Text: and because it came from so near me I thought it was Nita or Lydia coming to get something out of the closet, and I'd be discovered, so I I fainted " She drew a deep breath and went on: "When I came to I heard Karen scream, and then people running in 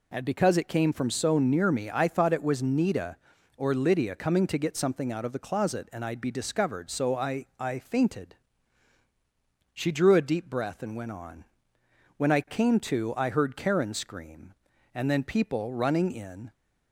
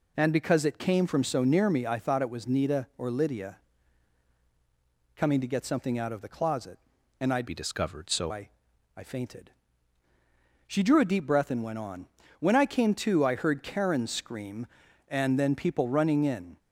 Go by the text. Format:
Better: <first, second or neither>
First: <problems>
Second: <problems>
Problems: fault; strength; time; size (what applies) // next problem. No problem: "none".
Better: first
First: none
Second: pauses between "Lydia" and "coming"; strong; at 3.5 s; 1.6 s long // changes voice from "be" to "so"; from 7.4 to 8.3 s; 0.9 s long // pauses between "I" and "I"; noticeable; at 8.4 s; 0.46 s long